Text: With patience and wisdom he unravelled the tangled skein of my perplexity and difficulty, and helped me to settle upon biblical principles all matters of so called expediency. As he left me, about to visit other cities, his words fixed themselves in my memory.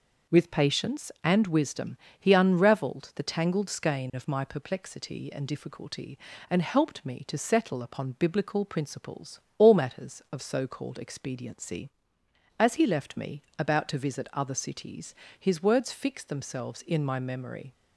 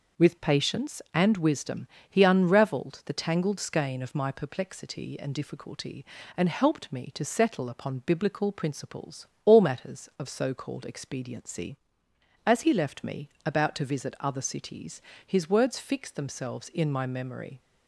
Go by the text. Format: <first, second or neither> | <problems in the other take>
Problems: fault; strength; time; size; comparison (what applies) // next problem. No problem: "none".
neither | pauses between "wisdom" and "he"; slight; the same in both // pauses between "principles" and "all"; slight; the same in both